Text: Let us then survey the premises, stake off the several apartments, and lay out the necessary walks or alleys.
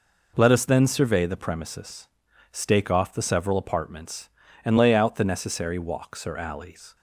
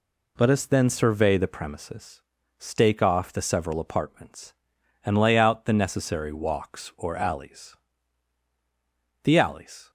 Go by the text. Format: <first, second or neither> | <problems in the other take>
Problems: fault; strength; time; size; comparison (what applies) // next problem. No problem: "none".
first | goes on to say "The alleys"; noticeable; from 9.2 s on; 0.68 s long